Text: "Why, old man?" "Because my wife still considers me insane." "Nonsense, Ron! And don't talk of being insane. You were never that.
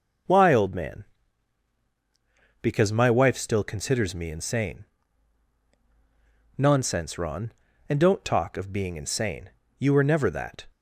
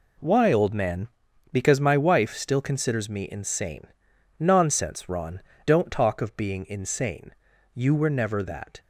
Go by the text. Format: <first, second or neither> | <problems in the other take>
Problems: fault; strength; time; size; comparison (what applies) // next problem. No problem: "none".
first | skips "And"; at 5.5 s